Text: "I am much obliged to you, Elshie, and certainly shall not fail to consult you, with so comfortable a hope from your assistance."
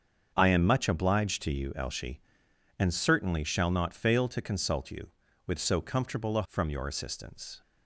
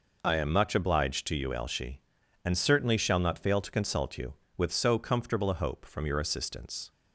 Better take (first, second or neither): second